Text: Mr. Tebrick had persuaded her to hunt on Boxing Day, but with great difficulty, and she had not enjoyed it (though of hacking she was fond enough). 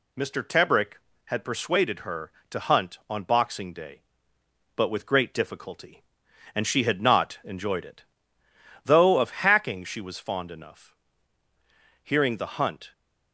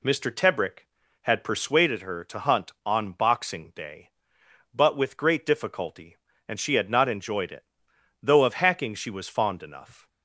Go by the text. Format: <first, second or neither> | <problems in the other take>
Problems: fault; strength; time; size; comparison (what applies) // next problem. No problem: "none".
second | goes on to say "Hearing the hunt"; noticeable; from 12.0 s on; 0.90 s long